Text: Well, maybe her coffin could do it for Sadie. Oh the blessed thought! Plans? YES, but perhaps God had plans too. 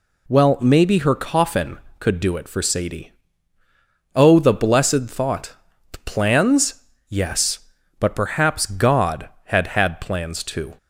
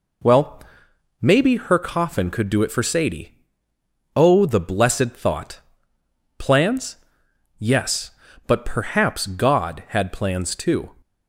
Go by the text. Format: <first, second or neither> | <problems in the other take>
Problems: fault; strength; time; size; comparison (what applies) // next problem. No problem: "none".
second | says "had" twice; at 9.6 s